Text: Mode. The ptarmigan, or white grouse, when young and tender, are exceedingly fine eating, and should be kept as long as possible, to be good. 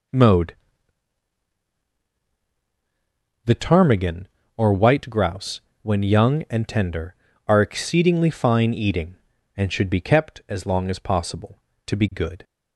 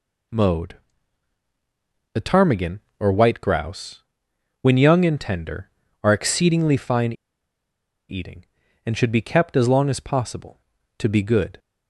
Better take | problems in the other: first | pauses between "fine" and "eating"; noticeable; at 7.1 s; 0.95 s long

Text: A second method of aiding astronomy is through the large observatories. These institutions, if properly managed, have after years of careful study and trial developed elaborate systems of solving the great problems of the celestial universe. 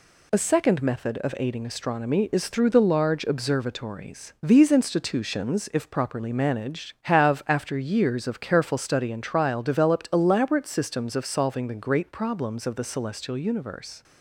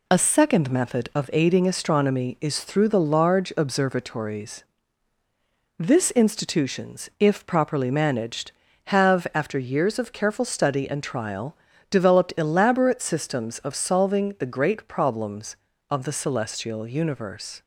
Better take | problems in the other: first | says "This" for "These"; at 5.7 s // pauses between "trial" and "developed"; slight; at 11.5 s; 0.34 s long

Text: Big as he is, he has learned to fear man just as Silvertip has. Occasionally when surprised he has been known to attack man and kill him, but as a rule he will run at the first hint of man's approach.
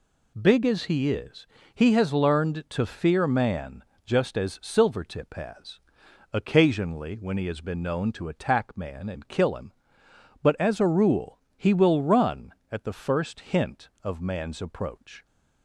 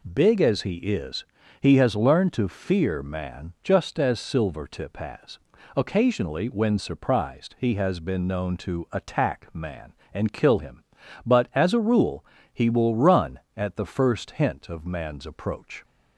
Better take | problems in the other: second | pauses between "man" and "just"; slight; at 3.8 s; 0.22 s long // skips "surprised"; at 7.3 s // pauses between "rule" and "he"; slight; at 11.3 s; 0.20 s long; slight in the second

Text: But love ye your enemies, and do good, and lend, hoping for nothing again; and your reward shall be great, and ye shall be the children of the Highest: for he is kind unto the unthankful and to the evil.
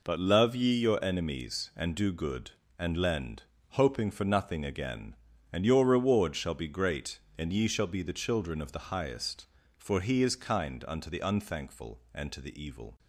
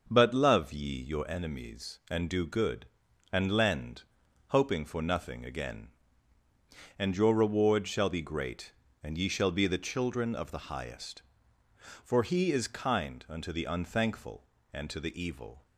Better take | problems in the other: neither | none

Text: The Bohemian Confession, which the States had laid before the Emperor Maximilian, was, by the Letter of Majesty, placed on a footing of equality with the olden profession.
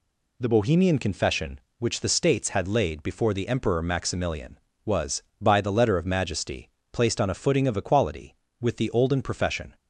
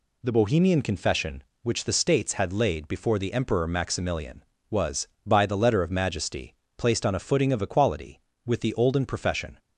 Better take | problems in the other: neither | none

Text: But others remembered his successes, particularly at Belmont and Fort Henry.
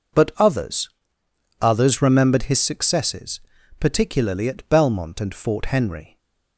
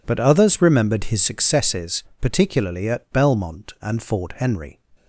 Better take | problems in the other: second | says "others" twice; at 1.6 s // stays silent after the last word; slight; from 6.0 s on; 0.5 s long

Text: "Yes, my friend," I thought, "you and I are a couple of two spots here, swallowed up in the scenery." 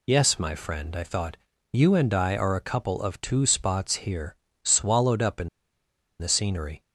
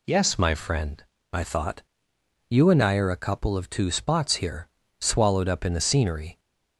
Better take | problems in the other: second | pauses between "in" and "the"; noticeable; at 5.4 s; 0.71 s long

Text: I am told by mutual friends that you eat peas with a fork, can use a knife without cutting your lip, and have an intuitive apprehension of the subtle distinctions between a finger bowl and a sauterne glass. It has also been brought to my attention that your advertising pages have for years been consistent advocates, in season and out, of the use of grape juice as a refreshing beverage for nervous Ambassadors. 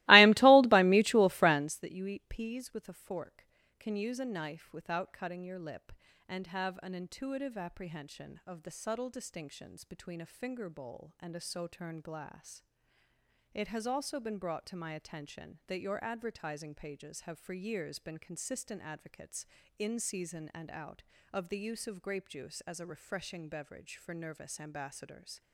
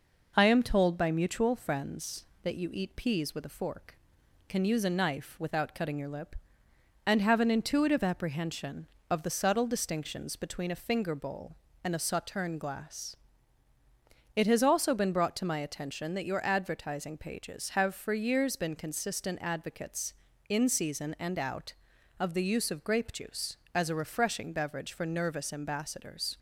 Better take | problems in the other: second | starts louder than the rest; strong; until 1.8 s; 21 dB

